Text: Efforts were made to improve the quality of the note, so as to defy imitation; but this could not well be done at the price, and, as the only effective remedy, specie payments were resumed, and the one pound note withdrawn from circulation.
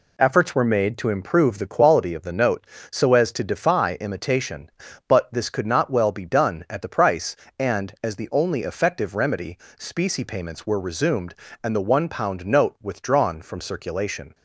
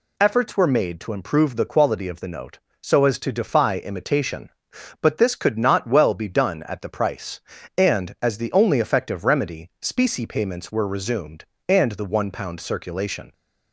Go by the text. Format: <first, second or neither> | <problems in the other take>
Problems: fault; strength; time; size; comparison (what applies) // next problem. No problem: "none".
first | skips "note withdrawn from"; at 12.6 s